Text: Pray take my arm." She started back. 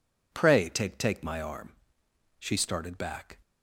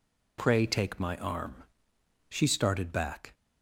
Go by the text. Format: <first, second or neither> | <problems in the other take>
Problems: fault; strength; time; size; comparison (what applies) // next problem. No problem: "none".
second | says "take" twice; at 0.9 s